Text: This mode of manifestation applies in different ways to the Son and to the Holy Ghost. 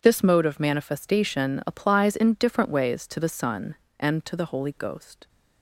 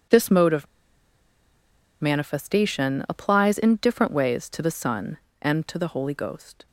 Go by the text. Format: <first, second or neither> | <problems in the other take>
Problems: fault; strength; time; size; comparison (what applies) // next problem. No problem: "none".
first | pauses between "of" and "manifestation"; strong; at 0.6 s; 1.3 s long